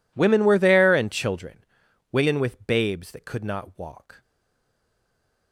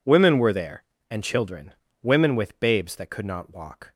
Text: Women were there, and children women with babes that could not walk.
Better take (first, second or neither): second